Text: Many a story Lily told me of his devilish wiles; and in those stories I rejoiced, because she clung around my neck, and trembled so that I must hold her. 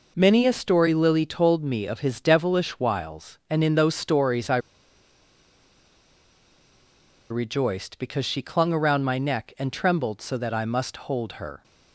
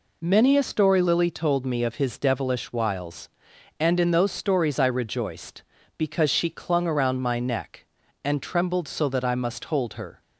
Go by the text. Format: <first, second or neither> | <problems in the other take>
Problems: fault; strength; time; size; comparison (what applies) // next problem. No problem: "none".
second | pauses between "I" and "rejoiced"; strong; at 4.5 s; 2.7 s long